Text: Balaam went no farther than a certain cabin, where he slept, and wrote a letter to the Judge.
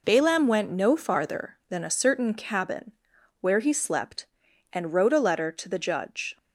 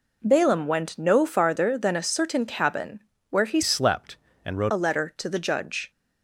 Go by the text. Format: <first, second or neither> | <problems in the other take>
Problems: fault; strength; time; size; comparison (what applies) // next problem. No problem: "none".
first | changes voice from "slept" to "wrote"; from 3.6 to 4.7 s; 1.1 s long